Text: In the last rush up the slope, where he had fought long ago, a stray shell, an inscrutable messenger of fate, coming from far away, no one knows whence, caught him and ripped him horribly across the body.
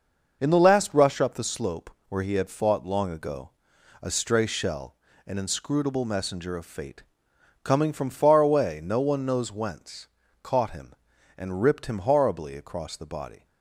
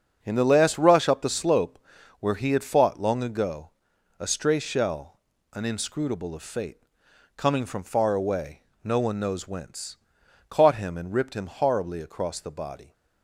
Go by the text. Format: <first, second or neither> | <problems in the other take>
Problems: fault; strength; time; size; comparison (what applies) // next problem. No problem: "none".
first | starts louder than the rest; until 1.2 s; 6.5 dB // skips "messenger"; at 6.3 s